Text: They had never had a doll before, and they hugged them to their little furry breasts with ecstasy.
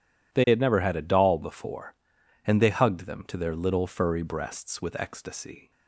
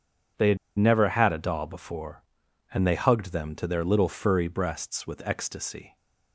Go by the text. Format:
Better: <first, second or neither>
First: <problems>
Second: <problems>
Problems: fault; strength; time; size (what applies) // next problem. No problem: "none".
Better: first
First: none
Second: pauses between "had" and "never"; slight; at 0.5 s; 0.20 s long